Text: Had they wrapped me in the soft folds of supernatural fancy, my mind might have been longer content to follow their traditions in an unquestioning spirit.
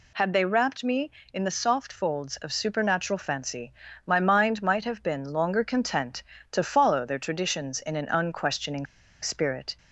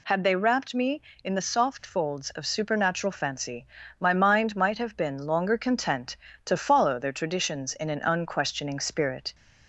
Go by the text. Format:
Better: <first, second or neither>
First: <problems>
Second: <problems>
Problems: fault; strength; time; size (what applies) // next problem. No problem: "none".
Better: second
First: pauses between "unquestioning" and "spirit"; at 8.8 s; 0.36 s long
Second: none